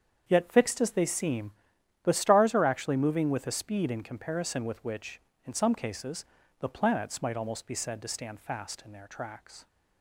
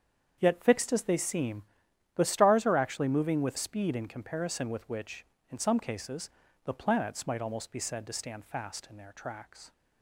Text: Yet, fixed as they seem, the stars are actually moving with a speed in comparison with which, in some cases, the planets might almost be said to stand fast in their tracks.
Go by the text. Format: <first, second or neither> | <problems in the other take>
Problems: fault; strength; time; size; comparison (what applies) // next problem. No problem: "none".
first | starts louder than the rest; strong; until 1.3 s; 7.5 dB; strong in the first // skips "a"; at 3.5 s